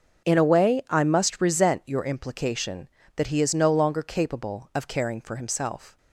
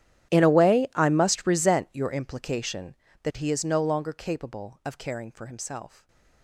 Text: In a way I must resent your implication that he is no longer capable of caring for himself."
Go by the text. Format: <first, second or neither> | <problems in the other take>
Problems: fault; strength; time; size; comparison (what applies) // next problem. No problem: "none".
first | gets quieter; strong; throughout; 24 dB // starts louder than the rest; strong; until 1.3 s; 12 dB; also in the first // stays silent after the last word; slight; from 5.8 s on; 0.6 s long